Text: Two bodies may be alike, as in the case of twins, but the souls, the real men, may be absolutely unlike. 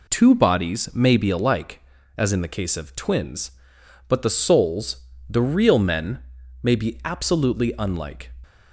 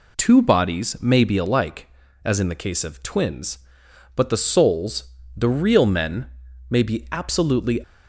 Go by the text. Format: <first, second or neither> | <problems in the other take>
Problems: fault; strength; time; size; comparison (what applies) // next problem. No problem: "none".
first | stops before "unlike"; at 7.8 s